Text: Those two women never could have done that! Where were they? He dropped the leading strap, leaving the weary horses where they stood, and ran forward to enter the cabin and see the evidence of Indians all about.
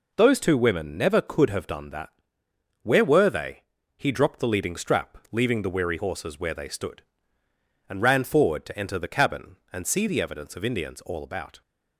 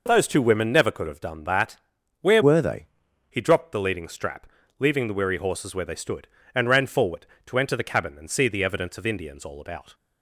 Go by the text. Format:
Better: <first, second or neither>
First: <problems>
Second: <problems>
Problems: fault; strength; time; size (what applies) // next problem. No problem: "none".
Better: first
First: none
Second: changes voice from "were" to "they"; from 2.4 to 2.8 s; 0.4 s long